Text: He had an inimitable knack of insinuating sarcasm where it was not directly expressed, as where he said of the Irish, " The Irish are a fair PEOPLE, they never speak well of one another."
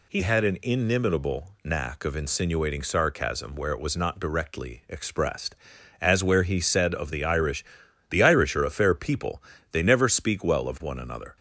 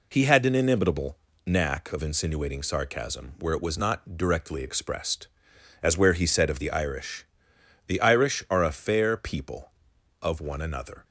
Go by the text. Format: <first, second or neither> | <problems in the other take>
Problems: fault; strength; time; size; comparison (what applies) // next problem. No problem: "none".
first | pauses between "inimitable" and "knack"; slight; at 1.1 s; 0.28 s long // skips "they never speak well"; at 9.9 s